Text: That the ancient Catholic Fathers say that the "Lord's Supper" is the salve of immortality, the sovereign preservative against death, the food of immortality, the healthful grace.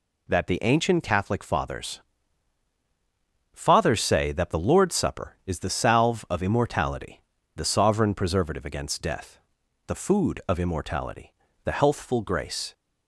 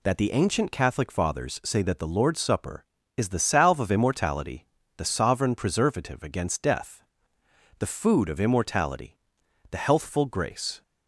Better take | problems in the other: second | says "Fathers" twice; at 3.5 s

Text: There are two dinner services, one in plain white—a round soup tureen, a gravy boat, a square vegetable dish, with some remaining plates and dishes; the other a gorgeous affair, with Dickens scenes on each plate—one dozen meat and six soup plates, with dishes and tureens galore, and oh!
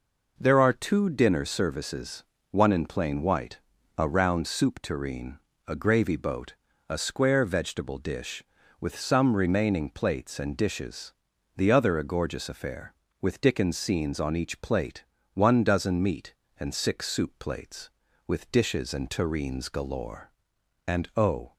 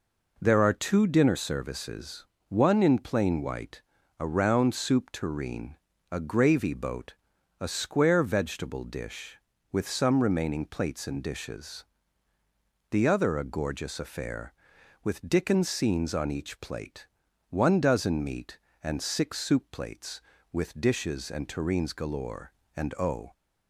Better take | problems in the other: neither | none

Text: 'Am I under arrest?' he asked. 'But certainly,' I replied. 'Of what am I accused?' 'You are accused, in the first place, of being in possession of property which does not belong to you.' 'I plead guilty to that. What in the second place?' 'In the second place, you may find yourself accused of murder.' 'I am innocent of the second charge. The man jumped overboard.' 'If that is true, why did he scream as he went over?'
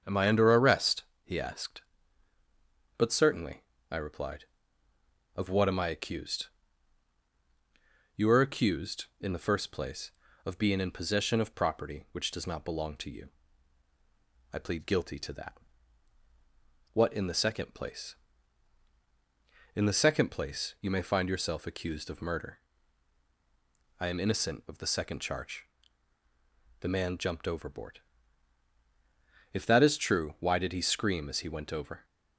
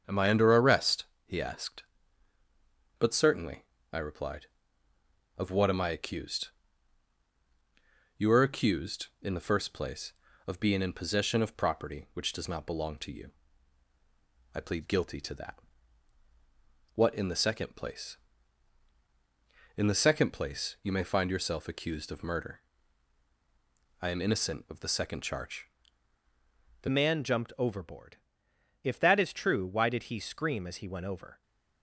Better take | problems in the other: first | starts louder than the rest; until 1.0 s; 7 dB; also in the first // changes voice at "man"; from 26.8 s on; 4.6 s long

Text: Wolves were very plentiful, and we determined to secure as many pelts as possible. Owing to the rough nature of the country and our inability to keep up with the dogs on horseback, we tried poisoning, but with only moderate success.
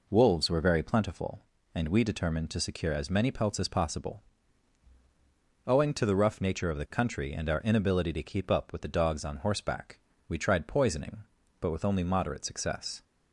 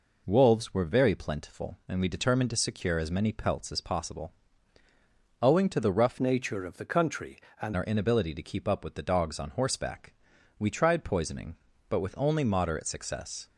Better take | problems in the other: first | changes voice from "nature" to "and"; from 6.1 to 7.7 s; 1.6 s long

